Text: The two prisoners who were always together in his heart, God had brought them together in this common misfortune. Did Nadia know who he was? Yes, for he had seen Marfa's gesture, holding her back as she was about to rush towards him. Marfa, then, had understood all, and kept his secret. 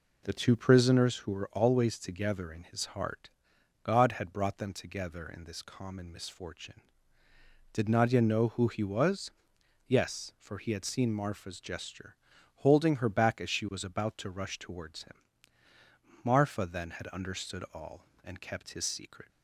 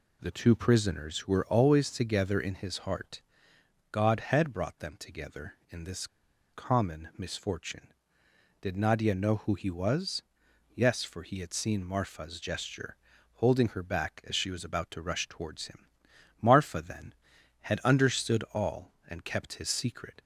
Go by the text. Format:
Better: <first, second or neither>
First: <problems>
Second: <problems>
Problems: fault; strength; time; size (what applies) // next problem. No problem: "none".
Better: first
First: none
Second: pauses between "this" and "common"; at 6.0 s; 0.45 s long